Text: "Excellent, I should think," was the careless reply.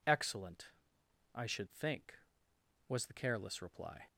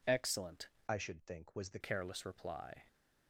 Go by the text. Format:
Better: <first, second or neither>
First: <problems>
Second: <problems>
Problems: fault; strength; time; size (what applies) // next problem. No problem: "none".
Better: first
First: none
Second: changes voice from "I" to "the"; from 0.8 to 1.7 s; 0.9 s long